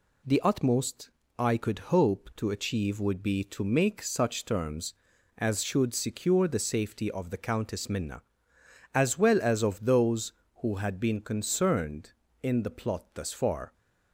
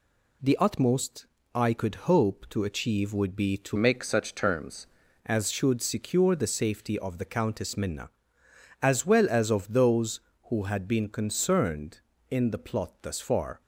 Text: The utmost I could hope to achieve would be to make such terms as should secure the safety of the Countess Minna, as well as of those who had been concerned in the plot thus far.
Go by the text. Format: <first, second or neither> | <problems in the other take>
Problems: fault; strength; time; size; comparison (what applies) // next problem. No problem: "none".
first | pauses between "utmost" and "I"; slight; at 1.2 s; 0.28 s long; slight in the first // changes voice from "make" to "terms"; from 3.7 to 4.8 s; 1.1 s long